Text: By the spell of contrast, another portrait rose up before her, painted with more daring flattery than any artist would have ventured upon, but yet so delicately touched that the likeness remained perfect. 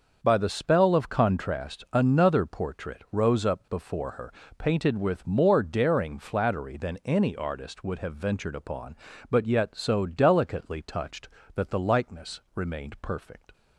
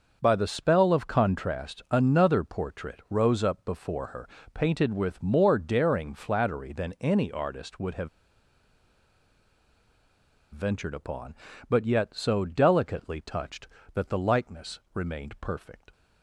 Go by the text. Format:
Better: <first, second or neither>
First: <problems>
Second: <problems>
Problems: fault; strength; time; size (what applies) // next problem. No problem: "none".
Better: first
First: starts louder than the rest; until 1.2 s; 6.5 dB // pauses between "likeness" and "remained"; slight; at 12.3 s; 0.16 s long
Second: starts louder than the rest; until 1.2 s; 6.5 dB // pauses between "have" and "ventured"; strong; at 8.0 s; 2.4 s long // pauses between "likeness" and "remained"; slight; at 14.7 s; 0.16 s long